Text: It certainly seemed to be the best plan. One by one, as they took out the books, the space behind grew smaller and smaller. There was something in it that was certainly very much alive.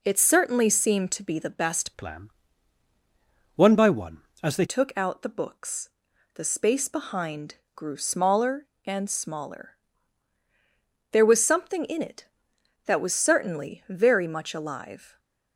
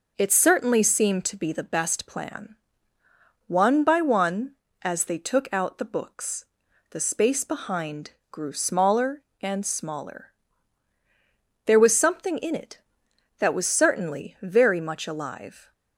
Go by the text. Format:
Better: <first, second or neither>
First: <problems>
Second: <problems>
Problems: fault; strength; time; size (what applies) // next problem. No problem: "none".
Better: second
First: changes voice from "plan" to "they"; from 1.9 to 4.6 s; 2.7 s long // pauses between "behind" and "grew"; slight; at 7.5 s; 0.18 s long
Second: pauses between "behind" and "grew"; slight; at 8.1 s; 0.18 s long